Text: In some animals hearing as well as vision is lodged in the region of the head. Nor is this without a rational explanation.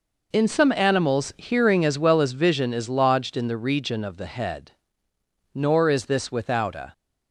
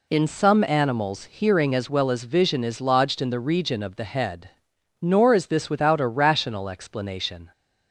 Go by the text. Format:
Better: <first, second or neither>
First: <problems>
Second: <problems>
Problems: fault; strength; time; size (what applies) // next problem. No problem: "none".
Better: second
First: stops before "rational explanation"; at 6.9 s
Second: none